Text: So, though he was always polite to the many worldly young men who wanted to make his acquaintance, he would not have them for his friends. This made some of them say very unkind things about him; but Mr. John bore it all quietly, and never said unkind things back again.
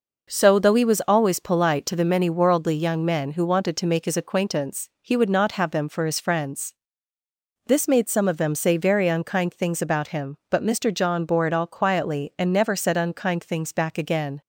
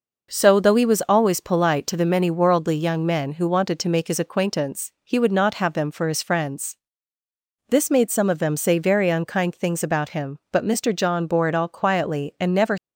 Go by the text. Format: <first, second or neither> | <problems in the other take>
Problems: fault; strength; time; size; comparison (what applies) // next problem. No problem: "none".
first | stops before "said unkind things back again"; at 12.7 s